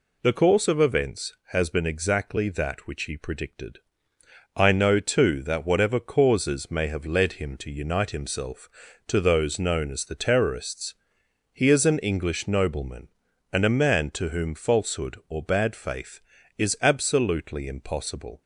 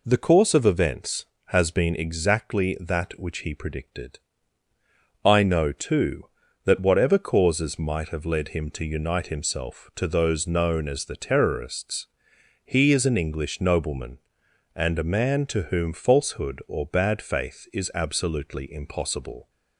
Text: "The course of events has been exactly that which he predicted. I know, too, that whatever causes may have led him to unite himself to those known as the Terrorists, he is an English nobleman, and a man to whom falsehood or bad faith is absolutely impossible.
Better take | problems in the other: first | says "might" for "may"; at 7.7 s

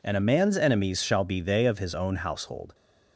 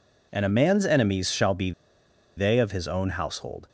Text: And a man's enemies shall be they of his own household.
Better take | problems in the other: first | pauses between "be" and "they"; noticeable; at 1.7 s; 0.65 s long

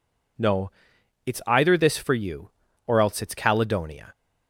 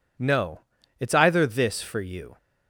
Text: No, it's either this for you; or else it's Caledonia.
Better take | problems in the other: first | stops before "or else it's Caledonia"; at 2.3 s

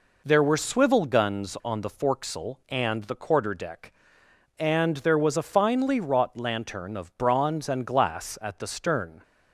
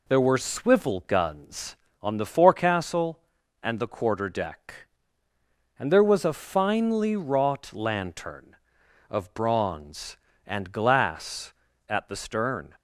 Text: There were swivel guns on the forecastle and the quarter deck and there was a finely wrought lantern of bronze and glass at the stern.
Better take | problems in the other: neither | none

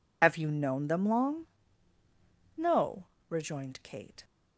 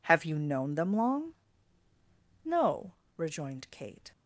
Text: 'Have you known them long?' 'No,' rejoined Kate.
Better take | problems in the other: second | loses the start of "Have"; at 0.2 s; 50 ms

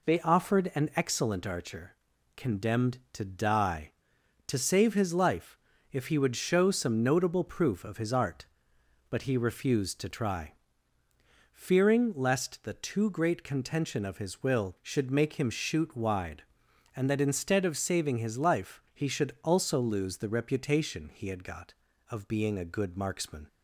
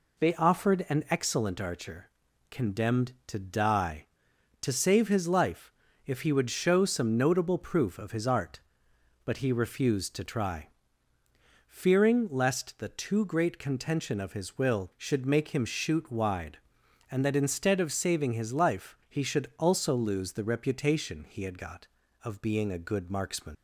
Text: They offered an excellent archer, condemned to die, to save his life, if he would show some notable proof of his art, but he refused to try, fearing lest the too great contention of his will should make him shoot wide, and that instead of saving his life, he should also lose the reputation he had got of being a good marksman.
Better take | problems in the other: first | leaves "marksman" unfinished; at 23.5 s; 55 ms

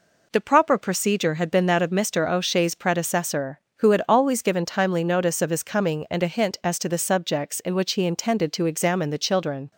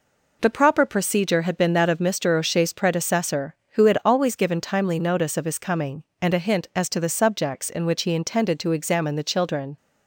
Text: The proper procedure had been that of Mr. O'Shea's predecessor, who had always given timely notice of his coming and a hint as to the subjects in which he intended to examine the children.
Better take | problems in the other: neither | none

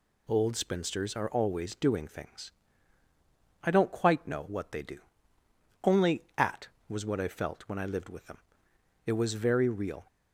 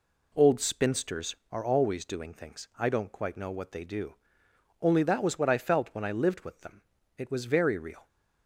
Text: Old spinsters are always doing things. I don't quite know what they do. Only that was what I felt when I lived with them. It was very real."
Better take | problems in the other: second | says "at" for "that"; at 6.3 s

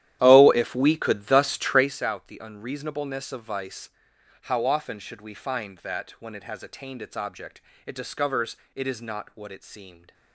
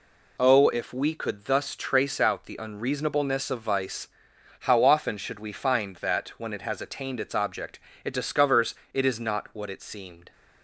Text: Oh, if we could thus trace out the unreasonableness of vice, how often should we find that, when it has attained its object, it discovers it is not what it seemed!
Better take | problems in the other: second | starts louder than the rest; strong; until 1.9 s; 12 dB // pauses between "discovers" and "it"; slight; at 8.5 s; 0.20 s long; slight in the second

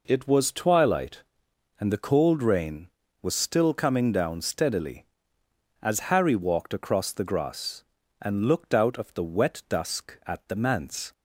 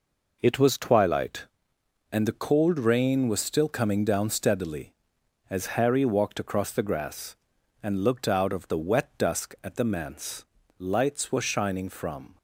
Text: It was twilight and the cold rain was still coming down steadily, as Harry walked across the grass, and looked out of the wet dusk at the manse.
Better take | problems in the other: first | goes on to say "Lights were shining from"; from 10.7 s on; 1.5 s long

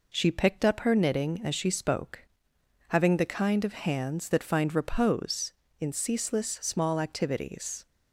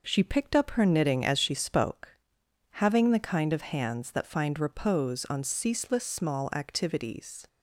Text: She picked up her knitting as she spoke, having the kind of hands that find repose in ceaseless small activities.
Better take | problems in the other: first | says "on" for "in"; at 5.3 s

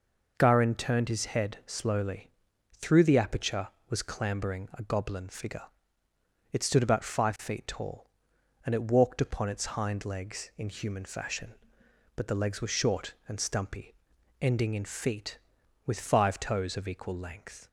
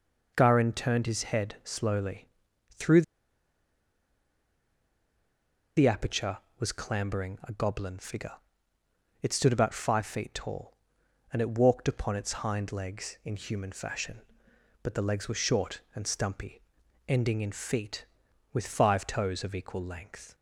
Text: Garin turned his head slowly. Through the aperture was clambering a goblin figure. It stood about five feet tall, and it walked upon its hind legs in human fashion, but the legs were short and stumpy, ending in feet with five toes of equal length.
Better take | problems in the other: first | pauses between "Through" and "the"; strong; at 3.0 s; 2.7 s long

